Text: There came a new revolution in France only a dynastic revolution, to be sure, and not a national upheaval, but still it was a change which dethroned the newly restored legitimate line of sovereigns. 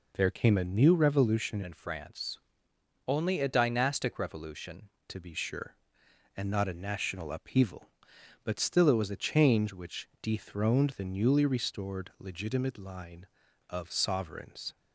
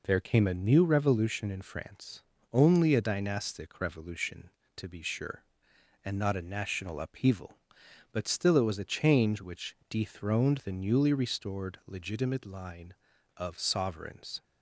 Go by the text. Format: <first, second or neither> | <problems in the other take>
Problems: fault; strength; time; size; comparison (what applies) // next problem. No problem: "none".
second | changes voice from "in" to "revolution"; from 1.6 to 4.8 s; 3.2 s long // pauses between "France" and "only"; noticeable; at 2.3 s; 0.70 s long; slight in the second